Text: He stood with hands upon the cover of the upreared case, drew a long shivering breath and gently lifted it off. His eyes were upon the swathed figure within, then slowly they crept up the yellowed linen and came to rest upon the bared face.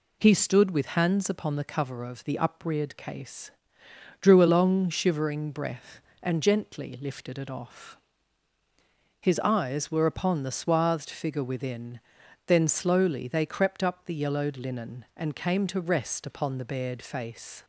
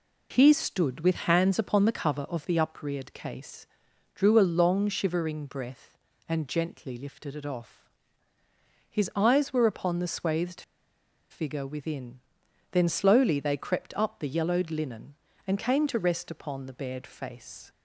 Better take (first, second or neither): first